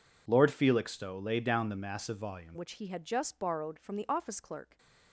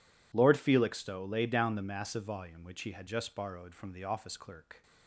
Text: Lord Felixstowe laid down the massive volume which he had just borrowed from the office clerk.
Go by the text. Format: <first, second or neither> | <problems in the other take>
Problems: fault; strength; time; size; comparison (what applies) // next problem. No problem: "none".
second | changes voice at "which"; from 2.5 s on; 2.2 s long